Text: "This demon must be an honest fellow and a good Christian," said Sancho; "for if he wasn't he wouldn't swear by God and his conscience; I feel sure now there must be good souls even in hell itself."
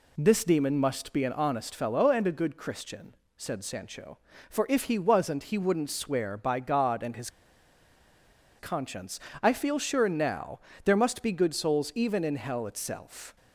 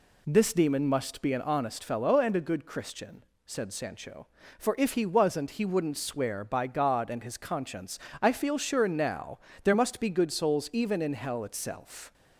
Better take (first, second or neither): second